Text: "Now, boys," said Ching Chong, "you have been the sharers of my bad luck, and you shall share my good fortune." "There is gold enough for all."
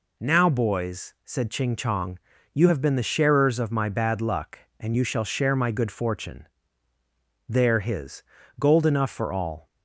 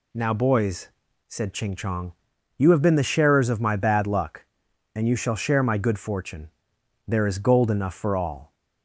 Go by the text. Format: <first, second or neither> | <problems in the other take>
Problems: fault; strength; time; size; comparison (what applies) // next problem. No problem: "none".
second | says "his" for "is"; at 7.7 s